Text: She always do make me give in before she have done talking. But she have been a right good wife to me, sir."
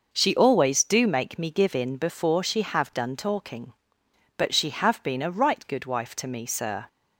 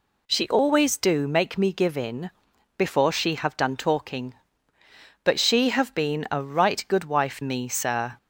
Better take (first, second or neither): first